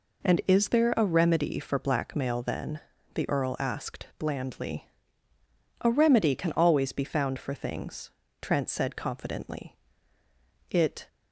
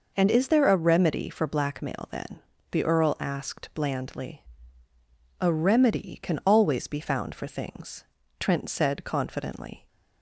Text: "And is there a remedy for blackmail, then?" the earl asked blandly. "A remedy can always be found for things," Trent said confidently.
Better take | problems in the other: second | goes on to say "It"; slight; from 10.6 s on; 0.38 s long

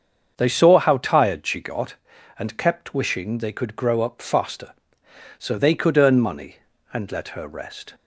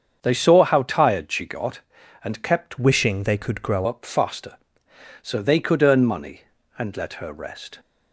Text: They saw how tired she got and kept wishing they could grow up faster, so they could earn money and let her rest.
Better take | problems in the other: first | starts louder than the rest; strong; until 1.2 s; 7 dB; also in the first // changes voice from "wishing" to "grow"; from 2.7 to 3.8 s; 1.1 s long

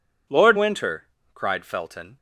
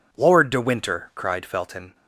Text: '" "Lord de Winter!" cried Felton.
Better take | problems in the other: second | skips "de"; at 0.5 s

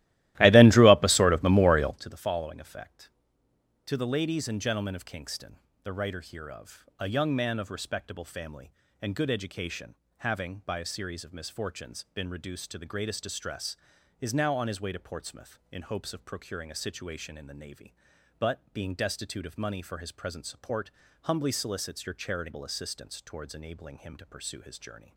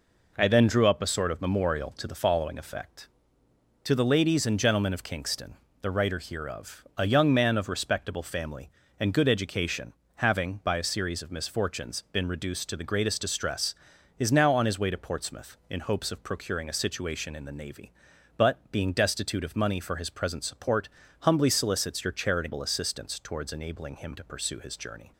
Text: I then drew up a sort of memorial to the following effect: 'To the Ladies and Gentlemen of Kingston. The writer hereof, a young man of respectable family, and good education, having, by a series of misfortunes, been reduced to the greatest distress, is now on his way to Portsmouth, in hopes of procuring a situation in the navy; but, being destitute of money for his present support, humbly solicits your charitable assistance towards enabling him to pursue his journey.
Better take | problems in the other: second | starts louder than the rest; strong; until 2.0 s; 16 dB

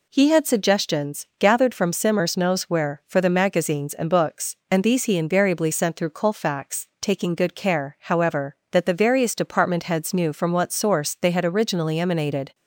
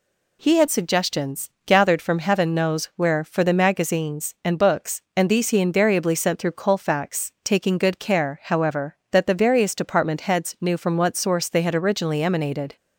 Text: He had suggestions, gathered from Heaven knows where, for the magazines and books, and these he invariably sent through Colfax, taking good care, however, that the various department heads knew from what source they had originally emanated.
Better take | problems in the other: second | says "Simmers" for "Heaven"; at 1.9 s

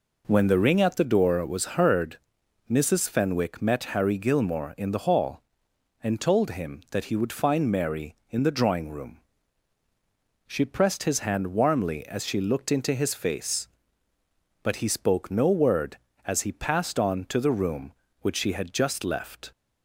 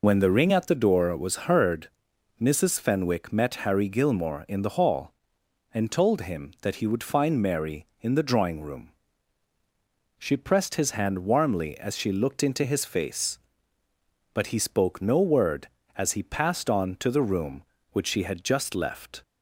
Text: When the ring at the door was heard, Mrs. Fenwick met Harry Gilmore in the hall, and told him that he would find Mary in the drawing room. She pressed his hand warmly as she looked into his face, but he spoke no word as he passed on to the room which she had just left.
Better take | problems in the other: first | loses the start of "When"; at 0.0 s; 65 ms

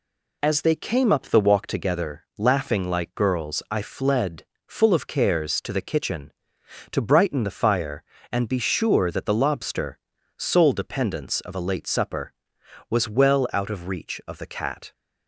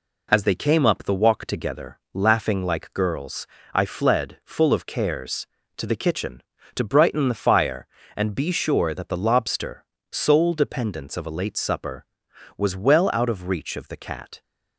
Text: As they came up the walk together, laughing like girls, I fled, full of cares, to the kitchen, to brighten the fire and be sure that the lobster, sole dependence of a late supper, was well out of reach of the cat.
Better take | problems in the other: neither | none

